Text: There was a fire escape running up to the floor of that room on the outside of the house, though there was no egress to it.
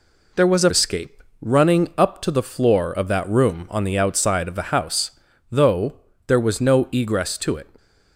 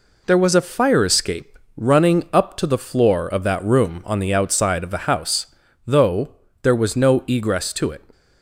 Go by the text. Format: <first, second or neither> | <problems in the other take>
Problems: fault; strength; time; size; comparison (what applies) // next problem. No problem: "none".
second | skips "fire"; at 0.7 s // pauses between "escape" and "running"; slight; at 1.2 s; 0.18 s long; slight in the second // pauses between "though" and "there"; slight; at 5.9 s; 0.32 s long; slight in the second